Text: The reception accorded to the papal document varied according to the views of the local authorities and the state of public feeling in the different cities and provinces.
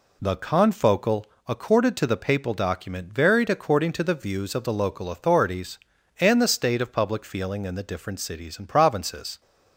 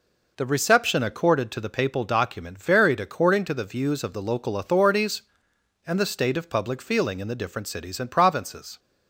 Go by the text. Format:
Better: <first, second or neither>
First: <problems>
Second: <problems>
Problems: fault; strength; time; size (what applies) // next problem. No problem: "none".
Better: second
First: says "confocal" for "reception"; at 0.3 s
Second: none